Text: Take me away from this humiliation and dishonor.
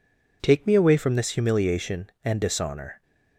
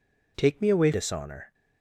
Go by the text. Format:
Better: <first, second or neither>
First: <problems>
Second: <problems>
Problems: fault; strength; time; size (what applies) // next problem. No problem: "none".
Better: first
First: none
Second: skips "from this humiliation and"; at 0.9 s